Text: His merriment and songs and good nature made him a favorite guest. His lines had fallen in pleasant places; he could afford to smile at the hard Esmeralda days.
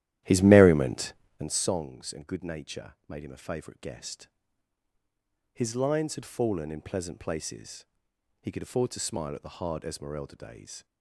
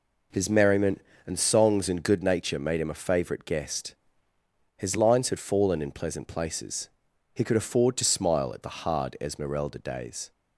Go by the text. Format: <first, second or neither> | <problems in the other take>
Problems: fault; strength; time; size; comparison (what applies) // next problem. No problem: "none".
second | starts louder than the rest; strong; until 1.6 s; 13 dB // pauses between "nature" and "made"; slight; at 2.9 s; 0.16 s long